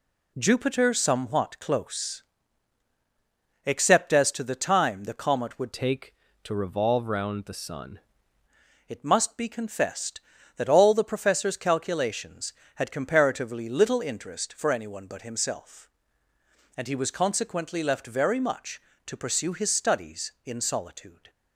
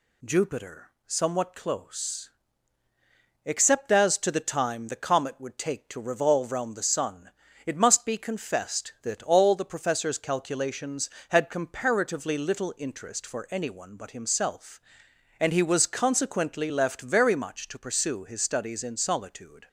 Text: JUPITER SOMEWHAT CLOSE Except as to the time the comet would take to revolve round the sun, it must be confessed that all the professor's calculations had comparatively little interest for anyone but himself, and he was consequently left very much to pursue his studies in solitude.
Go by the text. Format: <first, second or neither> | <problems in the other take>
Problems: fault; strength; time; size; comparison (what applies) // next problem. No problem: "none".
second | pauses between "CLOSE" and "Except"; strong; at 2.2 s; 1.4 s long; also in the second // changes voice from "take" to "sun"; from 5.7 to 7.9 s; 2.2 s long